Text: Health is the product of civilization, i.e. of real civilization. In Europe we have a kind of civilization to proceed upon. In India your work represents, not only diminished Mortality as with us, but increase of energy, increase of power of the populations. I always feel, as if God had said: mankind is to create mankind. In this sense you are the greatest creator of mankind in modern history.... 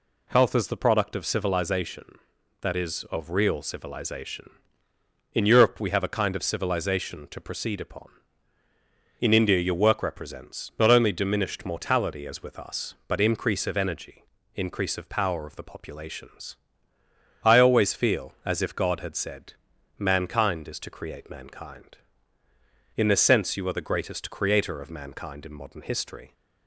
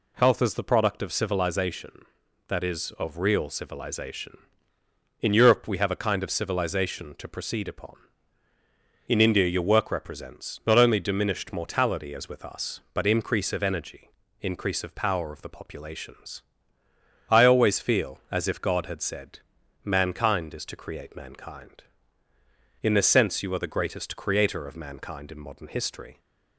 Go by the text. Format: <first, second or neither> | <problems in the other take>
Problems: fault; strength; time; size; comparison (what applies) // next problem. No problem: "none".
neither | none